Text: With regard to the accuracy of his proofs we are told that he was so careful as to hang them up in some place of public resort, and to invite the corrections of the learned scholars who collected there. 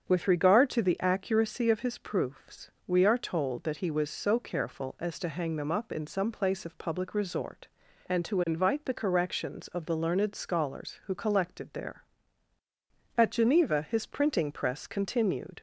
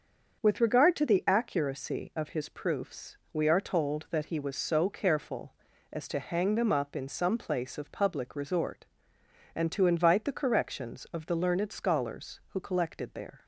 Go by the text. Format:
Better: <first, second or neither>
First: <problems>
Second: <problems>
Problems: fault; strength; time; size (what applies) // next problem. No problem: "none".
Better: second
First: starts louder than the rest; until 1.0 s; 7 dB // pauses between "proofs" and "we"; slight; at 2.6 s; 0.16 s long // goes on to say "At Geneva his printing press continued"; strong; from 13.1 s on; 2.4 s long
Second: starts louder than the rest; until 1.4 s; 6.5 dB // pauses between "proofs" and "we"; slight; at 3.1 s; 0.16 s long